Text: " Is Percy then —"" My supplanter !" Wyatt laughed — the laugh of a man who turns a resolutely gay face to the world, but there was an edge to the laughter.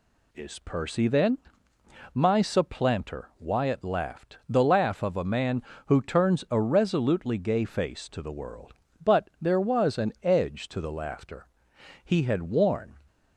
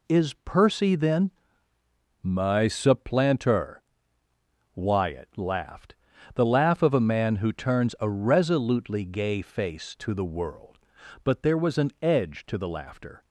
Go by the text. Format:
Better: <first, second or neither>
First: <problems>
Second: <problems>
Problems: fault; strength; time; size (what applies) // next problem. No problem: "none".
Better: second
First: goes on to say "He had worn"; noticeable; from 12.0 s on; 0.92 s long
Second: none